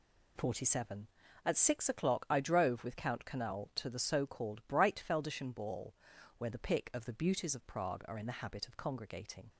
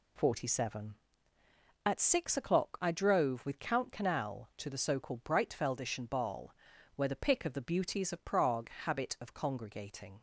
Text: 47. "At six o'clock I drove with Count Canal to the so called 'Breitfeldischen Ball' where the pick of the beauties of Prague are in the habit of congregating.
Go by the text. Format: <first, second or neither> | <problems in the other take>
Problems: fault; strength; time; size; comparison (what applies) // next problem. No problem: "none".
first | pauses between "Ball" and "where"; at 6.5 s; 0.42 s long; also in the first // skips "are in the"; at 8.7 s